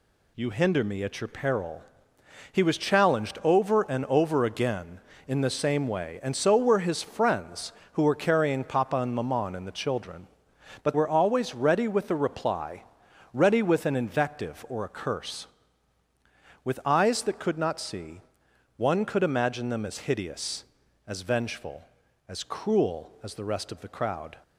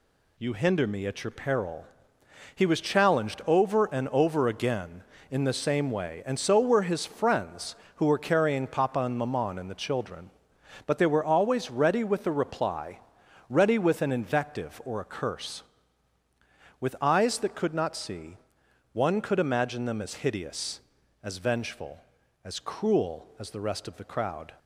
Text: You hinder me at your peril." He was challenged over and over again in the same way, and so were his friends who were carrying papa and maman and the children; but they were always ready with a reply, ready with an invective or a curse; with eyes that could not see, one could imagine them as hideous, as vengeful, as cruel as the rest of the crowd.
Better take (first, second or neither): second